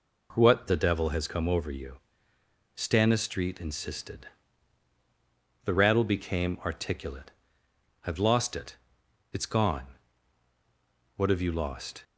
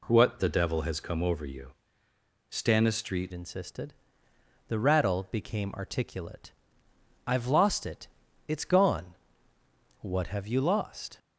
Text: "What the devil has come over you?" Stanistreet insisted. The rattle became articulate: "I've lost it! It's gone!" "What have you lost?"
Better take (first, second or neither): first